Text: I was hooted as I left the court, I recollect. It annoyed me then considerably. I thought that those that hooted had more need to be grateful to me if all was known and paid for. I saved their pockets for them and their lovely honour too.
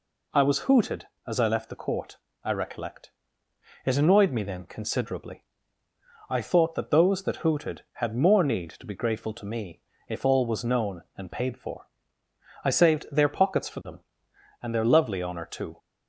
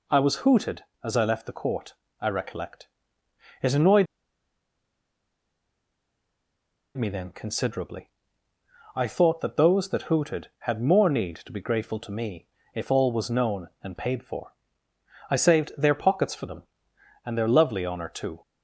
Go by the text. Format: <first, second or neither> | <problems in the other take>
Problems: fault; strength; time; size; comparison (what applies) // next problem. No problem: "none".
first | pauses between "annoyed" and "me"; strong; at 4.0 s; 2.9 s long // pauses between "me" and "if"; slight; at 12.4 s; 0.28 s long; slight in the first